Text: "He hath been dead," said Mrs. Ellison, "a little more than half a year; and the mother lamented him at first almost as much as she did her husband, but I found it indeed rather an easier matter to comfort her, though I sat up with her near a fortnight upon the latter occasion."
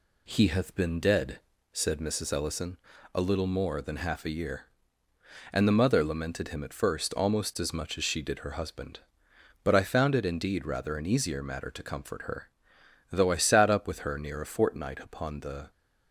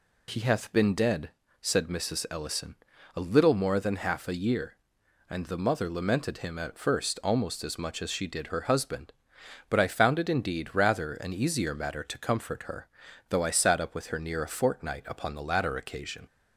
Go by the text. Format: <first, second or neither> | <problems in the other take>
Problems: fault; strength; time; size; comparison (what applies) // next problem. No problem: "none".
second | stops before "latter occasion"; at 15.7 s